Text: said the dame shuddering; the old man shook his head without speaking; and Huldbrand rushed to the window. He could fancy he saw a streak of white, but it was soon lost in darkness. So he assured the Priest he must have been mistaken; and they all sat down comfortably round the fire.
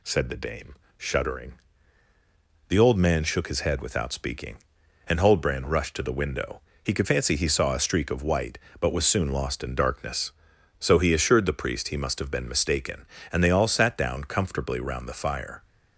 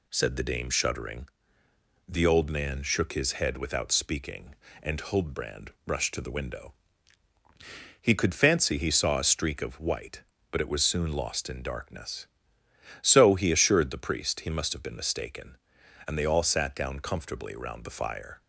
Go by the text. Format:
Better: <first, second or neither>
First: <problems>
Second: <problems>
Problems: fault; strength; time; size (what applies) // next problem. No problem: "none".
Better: second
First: pauses between "dame" and "shuddering"; slight; at 0.7 s; 0.24 s long // skips "it"; at 8.9 s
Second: none